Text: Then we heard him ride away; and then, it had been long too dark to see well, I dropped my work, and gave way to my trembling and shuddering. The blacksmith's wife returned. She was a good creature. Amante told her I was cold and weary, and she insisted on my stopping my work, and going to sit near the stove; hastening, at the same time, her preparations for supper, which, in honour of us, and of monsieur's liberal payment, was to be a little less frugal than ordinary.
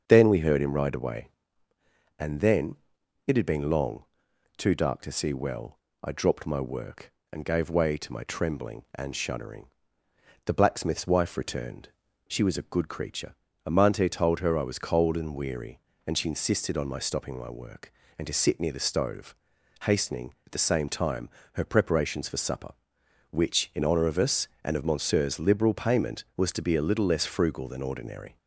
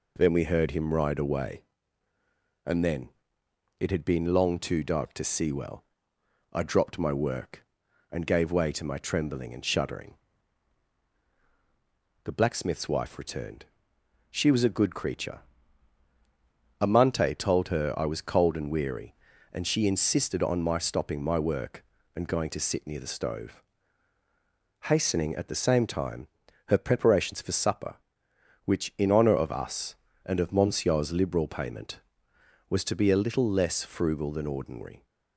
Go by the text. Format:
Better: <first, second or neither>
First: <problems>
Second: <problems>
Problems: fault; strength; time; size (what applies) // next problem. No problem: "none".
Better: second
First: starts louder than the rest; until 1.0 s; 7 dB // pauses between "long" and "too"; noticeable; at 4.0 s; 0.54 s long // skips "going"; at 18.2 s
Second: none